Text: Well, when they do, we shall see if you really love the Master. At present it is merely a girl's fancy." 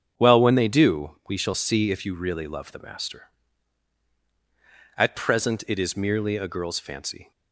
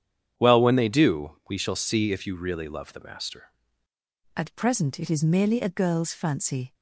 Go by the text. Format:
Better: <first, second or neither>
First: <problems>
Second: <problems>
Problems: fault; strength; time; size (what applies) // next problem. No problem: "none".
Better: first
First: starts louder than the rest; until 1.3 s; 7 dB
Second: starts louder than the rest; strong; until 1.5 s; 9 dB // changes voice at "At"; from 4.3 s on; 2.4 s long